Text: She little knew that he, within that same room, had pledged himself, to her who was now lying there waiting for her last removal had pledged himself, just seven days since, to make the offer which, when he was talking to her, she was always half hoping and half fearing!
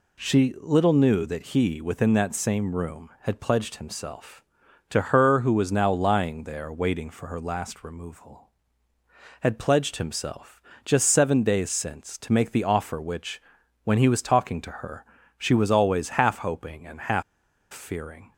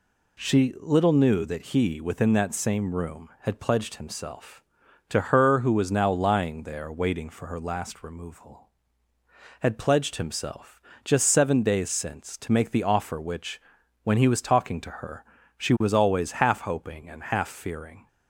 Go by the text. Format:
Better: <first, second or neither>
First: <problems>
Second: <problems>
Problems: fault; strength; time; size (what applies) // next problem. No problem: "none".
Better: second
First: pauses between "half" and "fearing"; noticeable; at 17.2 s; 0.49 s long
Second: none